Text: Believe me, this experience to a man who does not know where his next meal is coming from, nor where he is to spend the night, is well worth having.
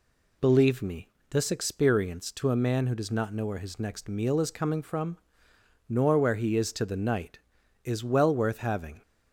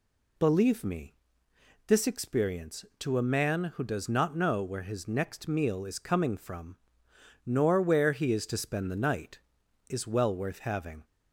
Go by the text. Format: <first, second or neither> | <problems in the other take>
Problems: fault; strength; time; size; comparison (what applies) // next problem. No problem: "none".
second | skips "spend"; at 6.8 s